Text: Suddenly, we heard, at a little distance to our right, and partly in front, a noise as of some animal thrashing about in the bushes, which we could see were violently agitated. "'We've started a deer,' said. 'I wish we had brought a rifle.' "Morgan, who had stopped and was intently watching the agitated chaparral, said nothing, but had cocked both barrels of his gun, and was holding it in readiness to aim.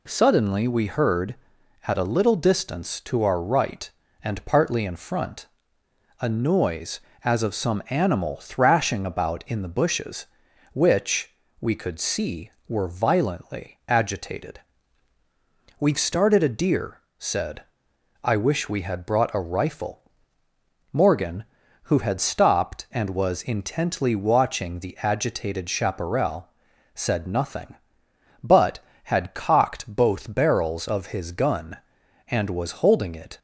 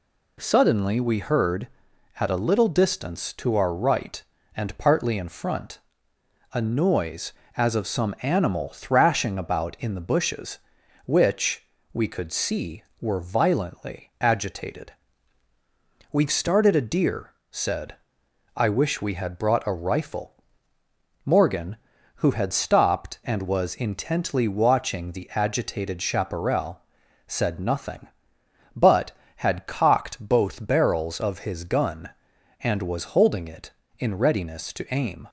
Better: second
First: pauses between "which" and "we"; slight; at 11.3 s; 0.26 s long // stops before "in readiness to aim"; at 33.3 s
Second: pauses between "which" and "we"; slight; at 11.6 s; 0.26 s long

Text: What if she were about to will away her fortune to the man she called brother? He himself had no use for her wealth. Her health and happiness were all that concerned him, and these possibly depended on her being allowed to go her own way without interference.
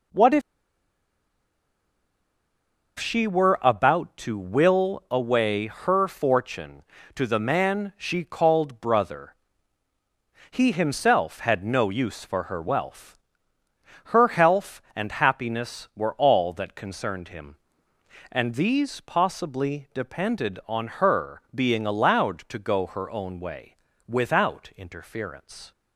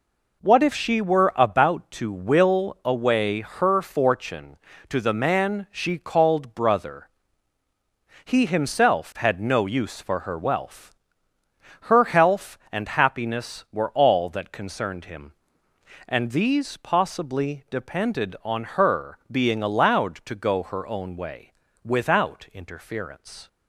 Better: second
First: pauses between "if" and "she"; strong; at 0.4 s; 2.5 s long // pauses between "way" and "without"; slight; at 23.7 s; 0.32 s long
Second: pauses between "way" and "without"; slight; at 21.5 s; 0.32 s long

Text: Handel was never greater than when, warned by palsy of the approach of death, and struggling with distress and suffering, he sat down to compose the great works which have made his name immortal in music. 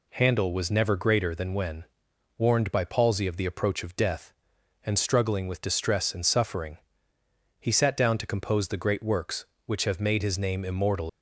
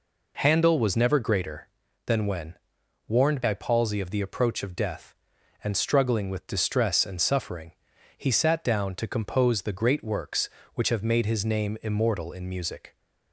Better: second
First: stops before "in music"; at 11.0 s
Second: none

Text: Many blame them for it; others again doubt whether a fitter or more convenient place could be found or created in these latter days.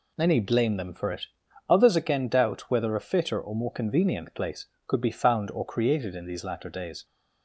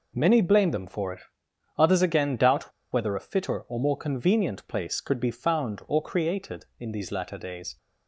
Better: first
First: none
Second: pauses between "doubt" and "whether"; slight; at 2.7 s; 0.21 s long

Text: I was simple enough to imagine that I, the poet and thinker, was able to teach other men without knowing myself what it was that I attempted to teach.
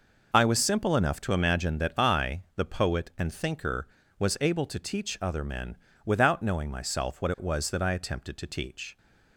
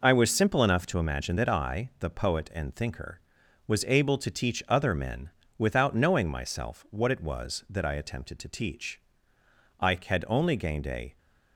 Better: first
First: pauses between "men" and "without"; slight; at 5.7 s; 0.30 s long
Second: pauses between "men" and "without"; slight; at 5.2 s; 0.28 s long // goes on to say "I had only gained a"; from 9.7 s on; 1.3 s long

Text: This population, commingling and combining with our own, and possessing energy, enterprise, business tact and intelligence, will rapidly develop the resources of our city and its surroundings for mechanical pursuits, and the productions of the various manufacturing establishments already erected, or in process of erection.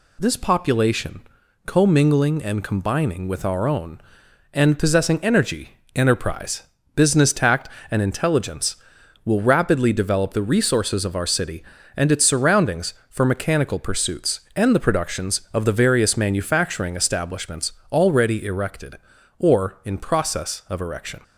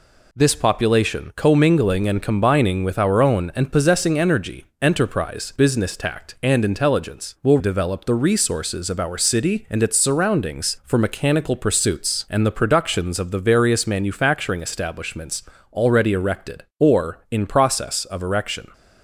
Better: first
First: pauses between "establishments" and "already"; slight; at 17.7 s; 0.22 s long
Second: skips "rapidly"; at 7.5 s // pauses between "establishments" and "already"; slight; at 15.4 s; 0.28 s long

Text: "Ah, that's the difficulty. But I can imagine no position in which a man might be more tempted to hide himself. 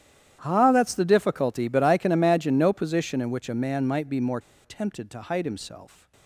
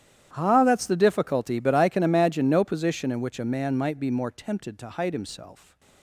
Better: second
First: starts louder than the rest; strong; until 1.4 s; 11 dB // pauses between "more" and "tempted"; slight; at 4.3 s; 0.24 s long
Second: starts louder than the rest; strong; until 1.3 s; 11 dB

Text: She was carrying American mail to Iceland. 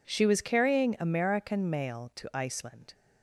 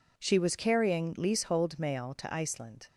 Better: first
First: none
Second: says "Leasehold" for "American"; at 1.1 s

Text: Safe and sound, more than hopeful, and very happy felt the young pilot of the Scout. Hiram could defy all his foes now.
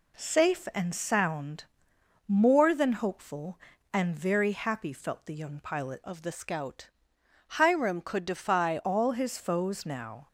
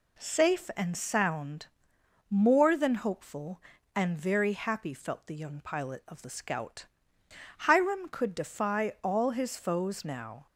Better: second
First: changes voice from "of" to "defy"; from 6.0 to 8.7 s; 2.7 s long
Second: none

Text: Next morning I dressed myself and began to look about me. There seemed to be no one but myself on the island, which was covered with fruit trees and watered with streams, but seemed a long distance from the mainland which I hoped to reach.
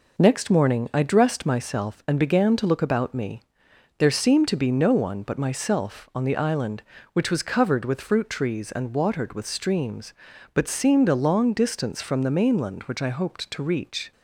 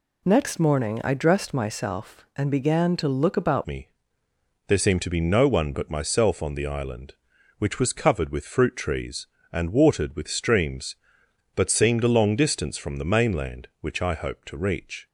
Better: first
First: none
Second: changes voice at "me"; from 3.6 s on; 11.4 s long

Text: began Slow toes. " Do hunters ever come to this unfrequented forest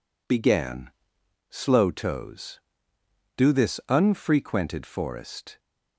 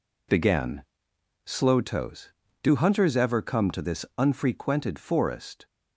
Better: second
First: pauses between "began" and "Slow"; noticeable; at 0.9 s; 0.60 s long // skips "hunters ever come to"; at 3.5 s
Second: pauses between "began" and "Slow"; noticeable; at 0.8 s; 0.64 s long

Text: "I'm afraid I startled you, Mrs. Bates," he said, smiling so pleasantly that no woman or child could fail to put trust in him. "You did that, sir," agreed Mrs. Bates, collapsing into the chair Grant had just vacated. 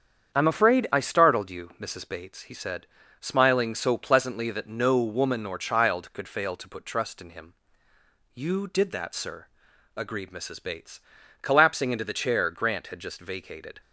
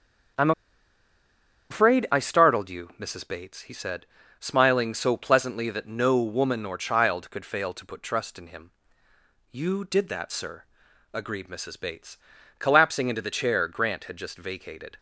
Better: first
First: starts louder than the rest; strong; until 1.3 s; 8 dB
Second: starts louder than the rest; strong; until 2.6 s; 7.5 dB // pauses between "I'm" and "afraid"; at 0.5 s; 1.1 s long

